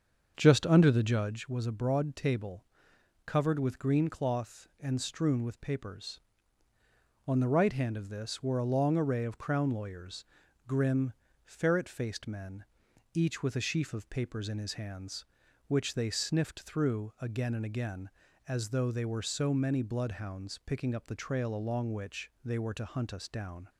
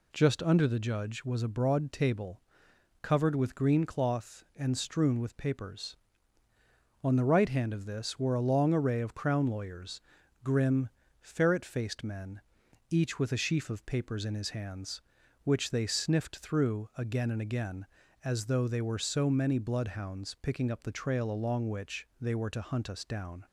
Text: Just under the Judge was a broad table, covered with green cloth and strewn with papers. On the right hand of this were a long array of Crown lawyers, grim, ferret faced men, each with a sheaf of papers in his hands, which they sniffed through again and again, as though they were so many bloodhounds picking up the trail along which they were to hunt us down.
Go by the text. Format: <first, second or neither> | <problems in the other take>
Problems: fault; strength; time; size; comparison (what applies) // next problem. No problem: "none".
second | starts louder than the rest; until 1.4 s; 7 dB